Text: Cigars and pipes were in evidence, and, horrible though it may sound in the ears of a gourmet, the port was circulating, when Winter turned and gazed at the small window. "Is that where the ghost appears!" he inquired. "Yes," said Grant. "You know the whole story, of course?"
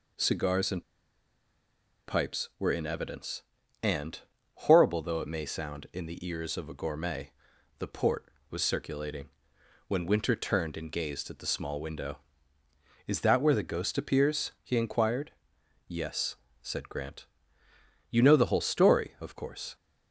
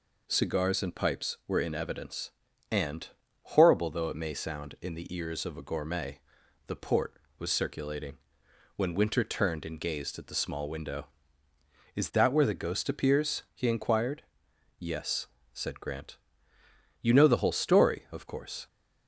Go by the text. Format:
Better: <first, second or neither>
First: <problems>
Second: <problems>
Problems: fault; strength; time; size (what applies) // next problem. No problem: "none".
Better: second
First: pauses between "and" and "pipes"; at 0.8 s; 1.2 s long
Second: none